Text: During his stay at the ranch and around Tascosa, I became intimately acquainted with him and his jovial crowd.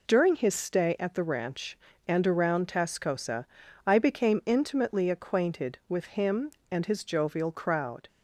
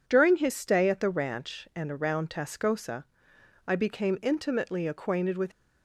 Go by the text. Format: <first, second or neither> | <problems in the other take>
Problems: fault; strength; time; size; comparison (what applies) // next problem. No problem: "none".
first | stops before "him and his jovial crowd"; at 5.5 s